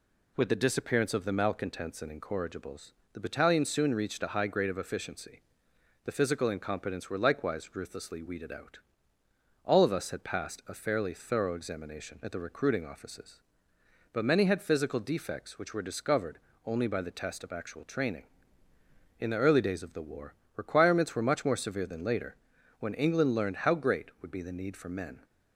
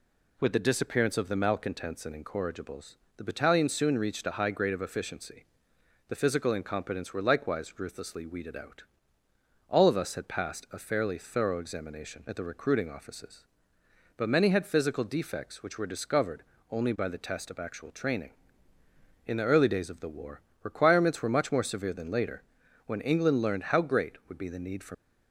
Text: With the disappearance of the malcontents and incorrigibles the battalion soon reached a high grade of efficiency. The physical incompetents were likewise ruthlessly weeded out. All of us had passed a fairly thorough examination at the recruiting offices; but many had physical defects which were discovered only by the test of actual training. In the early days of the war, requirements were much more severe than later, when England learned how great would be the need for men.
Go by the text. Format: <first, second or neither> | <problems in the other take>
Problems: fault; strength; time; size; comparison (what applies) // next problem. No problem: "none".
first | pauses between "incorrigibles" and "the"; slight; at 2.9 s; 0.20 s long; slight in the first // pauses between "discovered" and "only"; slight; at 16.4 s; 0.26 s long; slight in the first // stops before "men"; at 24.9 s